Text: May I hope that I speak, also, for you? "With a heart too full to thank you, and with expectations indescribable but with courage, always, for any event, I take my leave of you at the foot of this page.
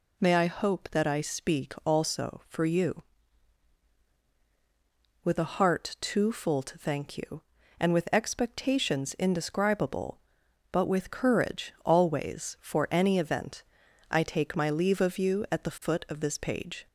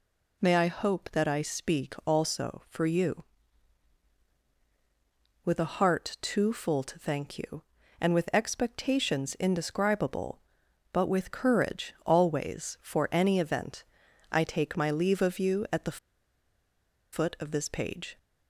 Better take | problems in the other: first | pauses between "the" and "foot"; at 15.9 s; 1.1 s long

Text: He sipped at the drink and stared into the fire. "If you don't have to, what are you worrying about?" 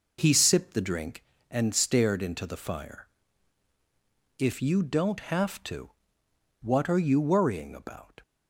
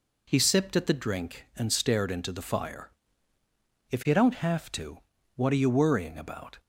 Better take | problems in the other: second | skips "at"; at 0.7 s

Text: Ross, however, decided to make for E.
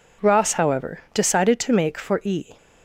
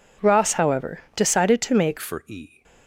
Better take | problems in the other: first | changes voice at "for"; from 1.9 s on; 0.7 s long

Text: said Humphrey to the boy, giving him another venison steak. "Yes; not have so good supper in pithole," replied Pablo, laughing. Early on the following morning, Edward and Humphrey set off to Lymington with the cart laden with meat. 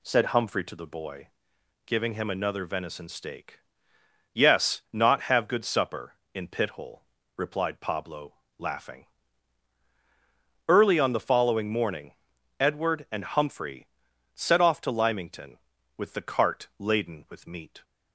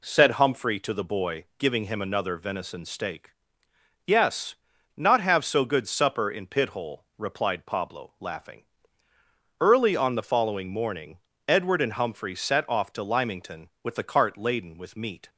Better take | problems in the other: second | skips "so"; at 5.4 s // pauses between "Humphrey" and "set"; noticeable; at 13.8 s; 0.46 s long

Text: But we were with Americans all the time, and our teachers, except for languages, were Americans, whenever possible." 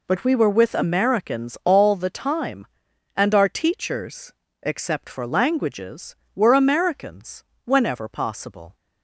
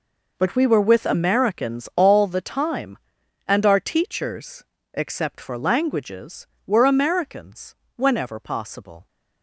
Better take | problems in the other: first | gets quieter; strong; throughout; 14.5 dB

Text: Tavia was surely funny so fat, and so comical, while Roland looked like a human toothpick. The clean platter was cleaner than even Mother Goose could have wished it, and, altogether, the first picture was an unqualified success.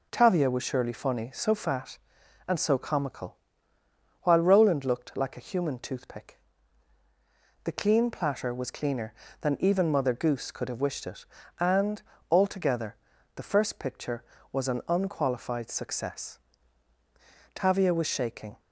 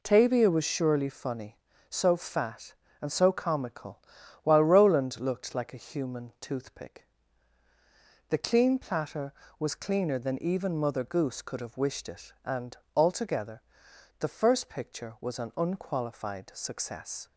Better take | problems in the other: second | goes on to say "Tavia was shaking"; noticeable; from 17.5 s on; 1.0 s long

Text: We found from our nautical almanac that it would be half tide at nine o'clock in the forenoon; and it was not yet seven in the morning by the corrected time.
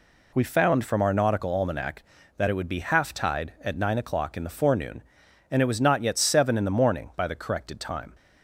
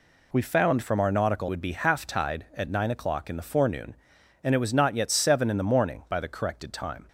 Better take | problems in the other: first | skips "almanac that it"; at 1.4 s

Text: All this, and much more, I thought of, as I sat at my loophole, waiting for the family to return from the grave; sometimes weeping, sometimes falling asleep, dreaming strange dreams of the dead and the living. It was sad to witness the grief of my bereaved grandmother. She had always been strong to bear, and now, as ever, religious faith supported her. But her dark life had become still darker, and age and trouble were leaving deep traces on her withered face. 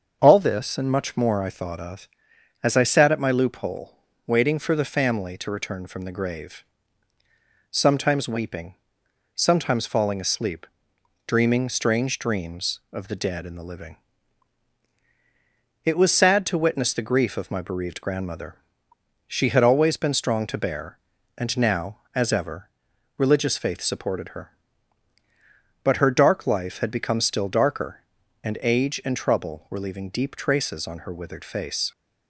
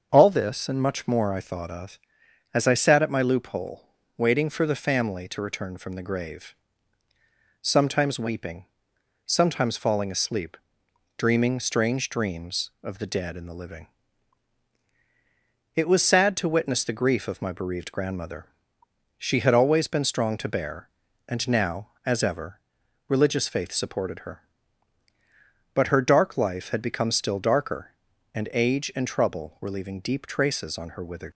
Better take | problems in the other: first | starts louder than the rest; until 1.1 s; 6.5 dB; also in the first // stops before "face"; at 31.3 s

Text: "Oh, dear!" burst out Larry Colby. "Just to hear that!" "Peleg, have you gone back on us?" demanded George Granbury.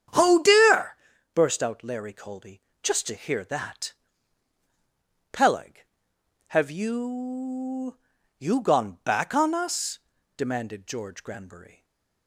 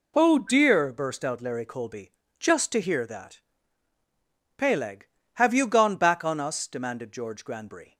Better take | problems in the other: second | starts louder than the rest; strong; until 1.5 s; 9 dB // says "you" twice; at 8.3 s // stays silent after the last word; slight; from 11.7 s on; 0.5 s long

